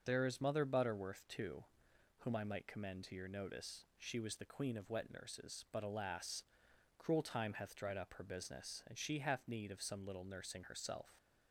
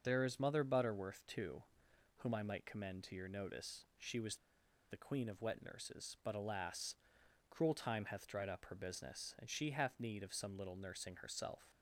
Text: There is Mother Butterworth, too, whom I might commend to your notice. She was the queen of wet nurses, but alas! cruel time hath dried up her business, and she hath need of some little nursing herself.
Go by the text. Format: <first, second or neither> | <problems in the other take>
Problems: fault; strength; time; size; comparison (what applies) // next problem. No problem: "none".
first | starts louder than the rest; noticeable; until 1.0 s; 6 dB; noticeable in the first // pauses between "was" and "the"; noticeable; at 4.3 s; 0.53 s long